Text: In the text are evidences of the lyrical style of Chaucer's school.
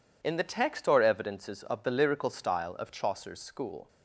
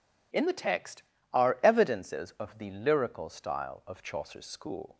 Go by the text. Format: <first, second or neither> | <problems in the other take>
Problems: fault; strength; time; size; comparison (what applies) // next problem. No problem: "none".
second | says "or" for "are"; at 0.8 s